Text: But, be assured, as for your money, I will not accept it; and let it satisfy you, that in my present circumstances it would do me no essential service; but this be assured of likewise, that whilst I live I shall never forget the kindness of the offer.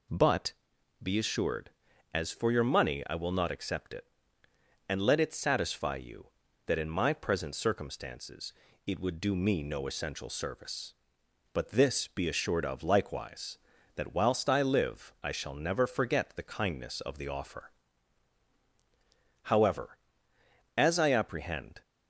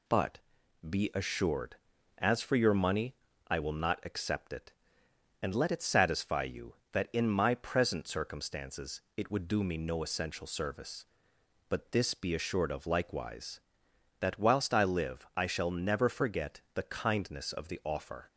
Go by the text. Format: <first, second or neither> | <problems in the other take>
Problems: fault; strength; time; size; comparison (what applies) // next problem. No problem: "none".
second | pauses between "circumstances" and "it"; slight; at 8.5 s; 0.36 s long; slight in the second // goes on to say "However as I apprehend"; strong; from 19.4 s on; 2.3 s long